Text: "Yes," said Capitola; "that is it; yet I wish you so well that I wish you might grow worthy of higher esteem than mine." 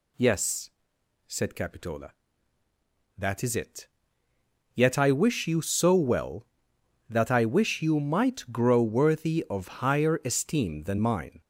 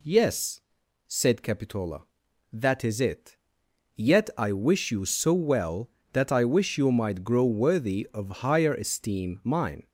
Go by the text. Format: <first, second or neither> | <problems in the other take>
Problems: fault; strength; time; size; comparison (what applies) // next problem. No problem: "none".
first | skips "than"; at 9.4 s